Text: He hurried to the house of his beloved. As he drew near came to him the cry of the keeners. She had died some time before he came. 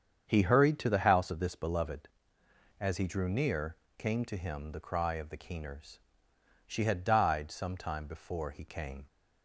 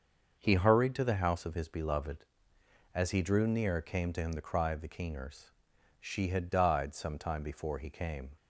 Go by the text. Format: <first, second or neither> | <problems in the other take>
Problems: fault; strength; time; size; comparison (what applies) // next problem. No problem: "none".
second | starts louder than the rest; strong; until 1.2 s; 7.5 dB; also in the second // says "this" for "his"; at 1.3 s // pauses between "near" and "came"; slight; at 3.7 s; 0.24 s long